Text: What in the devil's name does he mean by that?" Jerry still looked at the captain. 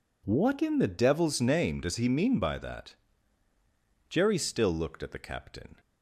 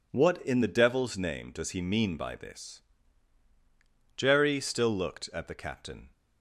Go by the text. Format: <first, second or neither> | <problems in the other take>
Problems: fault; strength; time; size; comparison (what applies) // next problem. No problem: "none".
first | says "this" for "that"; at 2.3 s